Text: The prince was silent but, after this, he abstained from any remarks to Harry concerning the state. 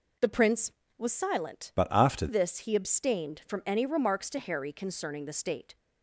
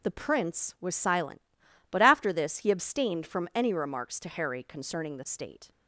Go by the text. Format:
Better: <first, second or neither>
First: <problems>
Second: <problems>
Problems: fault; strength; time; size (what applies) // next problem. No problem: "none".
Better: second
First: changes voice from "but" to "after"; from 1.7 to 2.2 s; 0.5 s long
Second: none